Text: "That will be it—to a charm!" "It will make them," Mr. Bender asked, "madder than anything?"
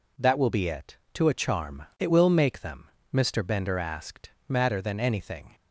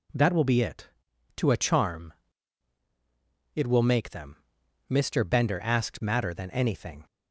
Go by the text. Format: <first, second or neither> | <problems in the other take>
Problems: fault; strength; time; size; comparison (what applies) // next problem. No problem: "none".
neither | none